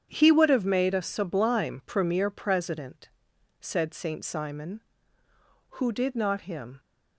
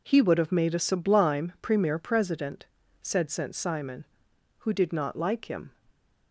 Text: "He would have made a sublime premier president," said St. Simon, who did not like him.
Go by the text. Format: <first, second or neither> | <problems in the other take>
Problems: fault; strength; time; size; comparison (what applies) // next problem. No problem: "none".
second | starts louder than the rest; strong; until 1.1 s; 8.5 dB // skips "like"; at 6.4 s